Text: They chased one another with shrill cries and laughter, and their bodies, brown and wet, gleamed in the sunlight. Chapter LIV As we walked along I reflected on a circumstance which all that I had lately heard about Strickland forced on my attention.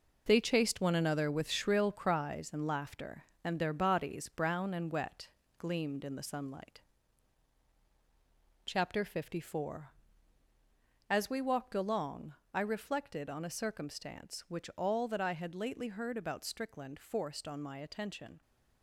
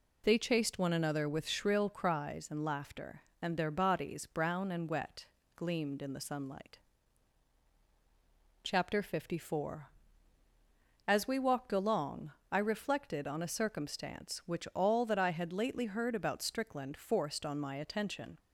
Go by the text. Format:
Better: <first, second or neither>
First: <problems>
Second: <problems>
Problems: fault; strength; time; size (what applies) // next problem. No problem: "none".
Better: second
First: gets quieter; strong; throughout; 8 dB // pauses between "along" and "I"; slight; at 12.3 s; 0.20 s long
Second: pauses between "along" and "I"; slight; at 12.3 s; 0.20 s long